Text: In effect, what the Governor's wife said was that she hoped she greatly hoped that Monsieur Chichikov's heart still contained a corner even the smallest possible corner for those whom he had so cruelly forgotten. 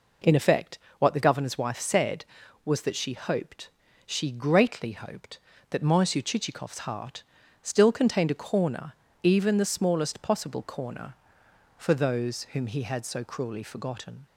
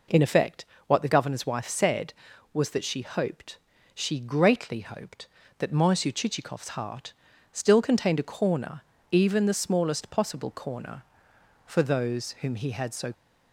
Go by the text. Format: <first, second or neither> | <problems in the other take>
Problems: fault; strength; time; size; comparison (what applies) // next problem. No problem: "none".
first | pauses between "hoped" and "she"; slight; at 3.5 s; 0.36 s long; slight in the first // pauses between "heart" and "still"; at 7.1 s; 0.38 s long; also in the first // pauses between "corner" and "even"; slight; at 8.8 s; 0.30 s long; slight in the first // stops before "cruelly forgotten"; at 13.1 s